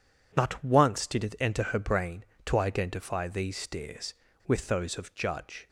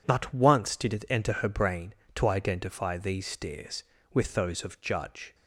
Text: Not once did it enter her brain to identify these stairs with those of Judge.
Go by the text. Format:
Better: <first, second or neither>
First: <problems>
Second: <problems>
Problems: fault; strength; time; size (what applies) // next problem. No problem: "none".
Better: neither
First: none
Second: none